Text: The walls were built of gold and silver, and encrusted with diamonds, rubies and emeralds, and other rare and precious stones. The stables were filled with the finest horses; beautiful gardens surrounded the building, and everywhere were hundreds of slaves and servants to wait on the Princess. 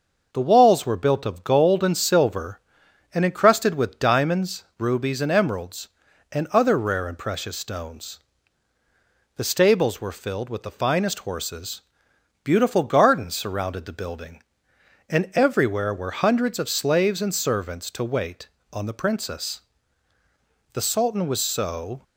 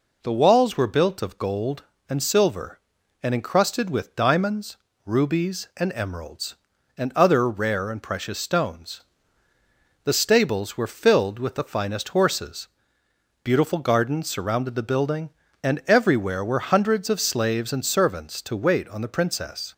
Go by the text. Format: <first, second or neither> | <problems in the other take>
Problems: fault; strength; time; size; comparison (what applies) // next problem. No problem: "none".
second | starts louder than the rest; until 1.3 s; 6 dB // goes on to say "The Sultan was so"; noticeable; from 20.7 s on; 1.3 s long